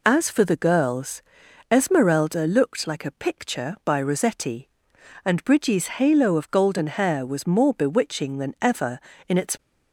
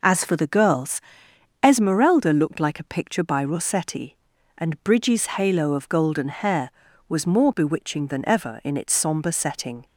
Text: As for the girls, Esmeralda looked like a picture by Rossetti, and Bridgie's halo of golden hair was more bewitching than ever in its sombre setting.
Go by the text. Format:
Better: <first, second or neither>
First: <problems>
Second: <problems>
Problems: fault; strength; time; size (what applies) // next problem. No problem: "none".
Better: second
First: stops before "sombre setting"; at 9.5 s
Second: none